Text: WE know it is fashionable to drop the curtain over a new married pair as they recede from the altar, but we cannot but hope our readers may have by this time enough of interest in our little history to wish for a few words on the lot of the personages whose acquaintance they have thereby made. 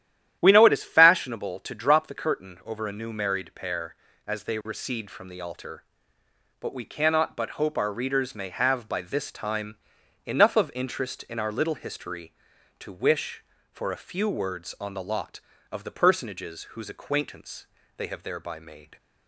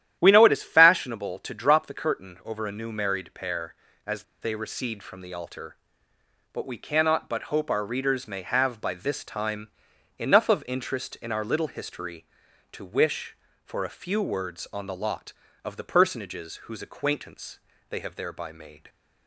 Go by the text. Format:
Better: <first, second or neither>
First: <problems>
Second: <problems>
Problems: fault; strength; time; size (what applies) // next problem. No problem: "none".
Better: first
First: starts louder than the rest; strong; until 1.4 s; 11 dB // pauses between "time" and "enough"; noticeable; at 9.7 s; 0.48 s long // pauses between "acquaintance" and "they"; slight; at 17.6 s; 0.32 s long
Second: starts louder than the rest; strong; until 1.2 s; 11 dB // pauses between "as" and "they"; slight; at 4.2 s; 0.19 s long // pauses between "time" and "enough"; noticeable; at 9.6 s; 0.48 s long // pauses between "acquaintance" and "they"; slight; at 17.5 s; 0.32 s long